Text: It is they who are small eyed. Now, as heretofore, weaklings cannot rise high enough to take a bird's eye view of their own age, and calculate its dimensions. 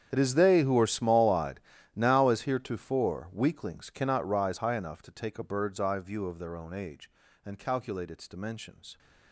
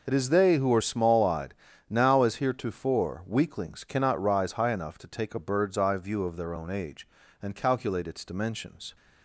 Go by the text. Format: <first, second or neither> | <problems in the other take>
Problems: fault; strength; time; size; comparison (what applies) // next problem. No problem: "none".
second | gets quieter; strong; throughout; 20 dB